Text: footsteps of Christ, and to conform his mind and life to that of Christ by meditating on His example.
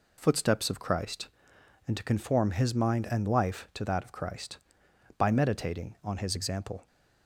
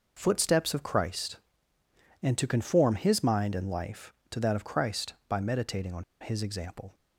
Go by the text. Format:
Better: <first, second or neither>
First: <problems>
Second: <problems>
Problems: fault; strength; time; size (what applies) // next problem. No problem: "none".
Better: first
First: none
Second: pauses between "on" and "His"; slight; at 6.0 s; 0.19 s long